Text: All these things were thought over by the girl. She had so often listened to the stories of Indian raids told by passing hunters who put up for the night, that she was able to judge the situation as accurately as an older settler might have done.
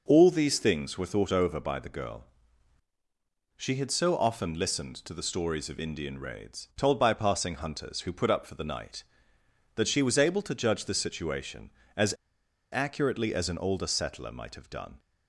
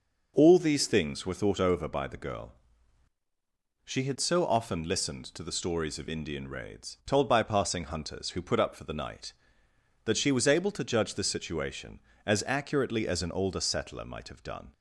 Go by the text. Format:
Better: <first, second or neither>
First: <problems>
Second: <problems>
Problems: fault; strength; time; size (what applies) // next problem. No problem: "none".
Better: second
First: pauses between "as" and "accurately"; noticeable; at 12.1 s; 0.57 s long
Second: none